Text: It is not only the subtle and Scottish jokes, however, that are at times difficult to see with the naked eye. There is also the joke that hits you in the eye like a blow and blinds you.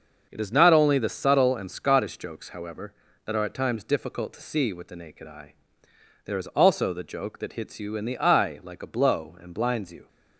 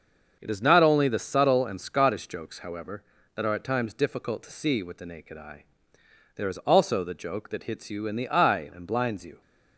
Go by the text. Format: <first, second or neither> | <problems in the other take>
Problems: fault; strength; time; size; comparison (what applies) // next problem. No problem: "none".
first | starts louder than the rest; until 1.4 s; 6.5 dB; also in the first // skips "like a blow"; at 8.7 s